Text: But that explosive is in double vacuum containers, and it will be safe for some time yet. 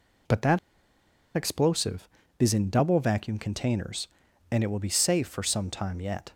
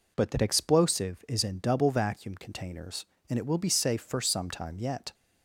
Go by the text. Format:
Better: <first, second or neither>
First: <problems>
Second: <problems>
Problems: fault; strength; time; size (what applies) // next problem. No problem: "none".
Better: second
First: pauses between "that" and "explosive"; noticeable; at 0.5 s; 0.77 s long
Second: none